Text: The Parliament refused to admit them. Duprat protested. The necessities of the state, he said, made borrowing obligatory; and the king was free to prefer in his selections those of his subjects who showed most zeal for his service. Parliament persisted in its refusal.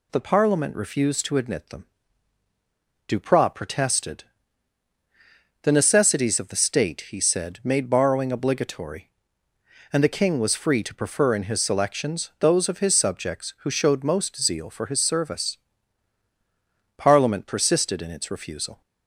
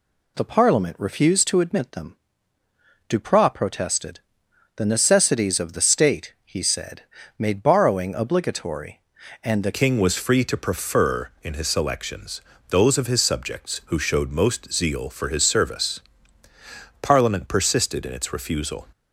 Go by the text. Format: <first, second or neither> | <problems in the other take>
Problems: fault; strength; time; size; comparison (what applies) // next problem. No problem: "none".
first | changes voice at "king"; from 9.7 s on; 9.1 s long // pauses between "selections" and "those"; slight; at 12.4 s; 0.26 s long